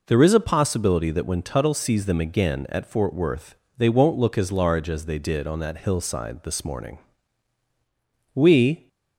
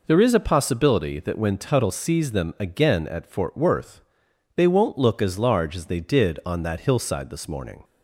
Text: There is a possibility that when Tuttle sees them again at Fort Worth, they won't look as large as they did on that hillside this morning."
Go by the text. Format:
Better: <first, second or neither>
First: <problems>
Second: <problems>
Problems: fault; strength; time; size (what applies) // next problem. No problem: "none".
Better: second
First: goes on to say "We"; from 8.3 s on; 0.54 s long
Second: none